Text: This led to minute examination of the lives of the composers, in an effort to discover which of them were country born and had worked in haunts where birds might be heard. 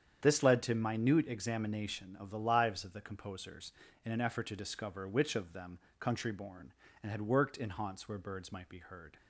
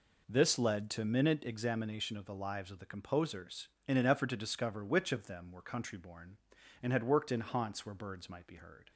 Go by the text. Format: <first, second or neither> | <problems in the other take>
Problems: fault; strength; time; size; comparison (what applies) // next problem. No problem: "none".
second | starts louder than the rest; strong; until 1.2 s; 8.5 dB // skips "were"; at 5.8 s